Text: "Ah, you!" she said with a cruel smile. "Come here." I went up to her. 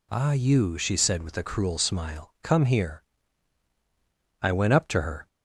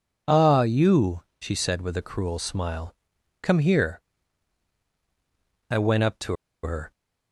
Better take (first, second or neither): first